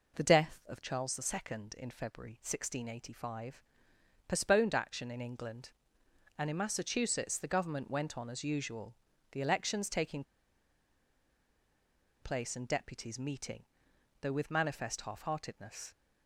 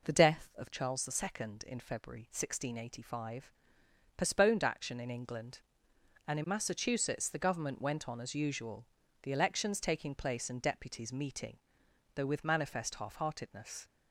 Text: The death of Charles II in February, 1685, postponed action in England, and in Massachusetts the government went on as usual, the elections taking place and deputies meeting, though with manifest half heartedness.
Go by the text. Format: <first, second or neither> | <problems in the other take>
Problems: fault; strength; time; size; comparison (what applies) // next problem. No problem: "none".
second | pauses between "taking" and "place"; strong; at 10.2 s; 2.0 s long